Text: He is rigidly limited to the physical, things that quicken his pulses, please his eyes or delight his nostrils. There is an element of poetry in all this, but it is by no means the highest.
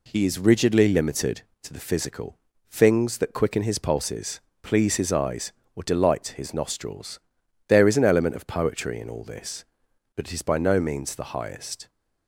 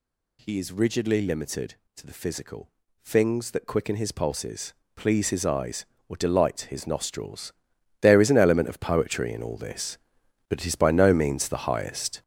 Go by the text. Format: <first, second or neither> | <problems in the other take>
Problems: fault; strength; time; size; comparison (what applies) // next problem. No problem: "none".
first | gets louder; throughout; 6.5 dB